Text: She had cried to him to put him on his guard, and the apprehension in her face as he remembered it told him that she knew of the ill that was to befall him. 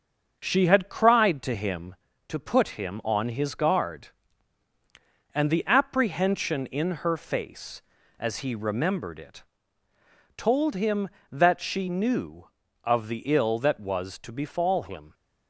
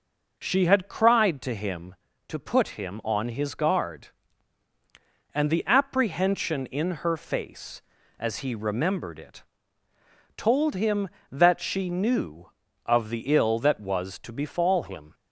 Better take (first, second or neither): second